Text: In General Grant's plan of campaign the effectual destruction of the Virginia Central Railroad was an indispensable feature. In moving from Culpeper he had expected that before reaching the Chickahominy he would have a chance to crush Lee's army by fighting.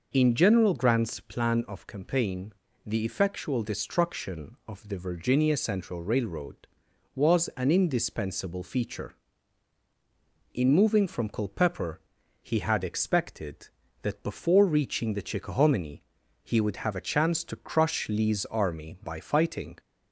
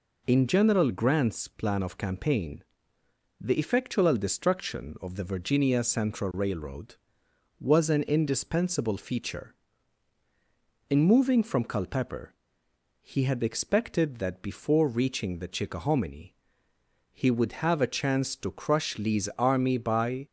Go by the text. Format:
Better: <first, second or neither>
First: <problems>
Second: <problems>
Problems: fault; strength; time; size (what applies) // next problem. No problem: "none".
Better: first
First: pauses between "campaign" and "the"; slight; at 2.5 s; 0.32 s long // pauses between "Culpeper" and "he"; at 11.9 s; 0.42 s long // pauses between "Chickahominy" and "he"; at 16.0 s; 0.38 s long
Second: pauses between "campaign" and "the"; noticeable; at 2.6 s; 0.78 s long // pauses between "Culpeper" and "he"; noticeable; at 12.3 s; 0.70 s long // pauses between "Chickahominy" and "he"; noticeable; at 16.3 s; 0.78 s long // stops before "fighting"; at 20.2 s